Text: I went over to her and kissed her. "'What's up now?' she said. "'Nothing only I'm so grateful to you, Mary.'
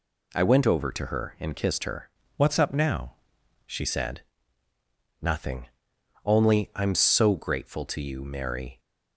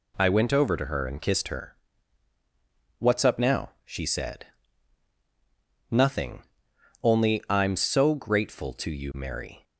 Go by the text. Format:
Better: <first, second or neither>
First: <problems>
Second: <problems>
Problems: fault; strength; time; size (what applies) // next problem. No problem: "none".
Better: second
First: changes voice from "What's" to "she"; from 2.3 to 3.8 s; 1.5 s long // pauses between "Nothing" and "only"; noticeable; at 5.6 s; 0.58 s long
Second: pauses between "Nothing" and "only"; noticeable; at 6.4 s; 0.60 s long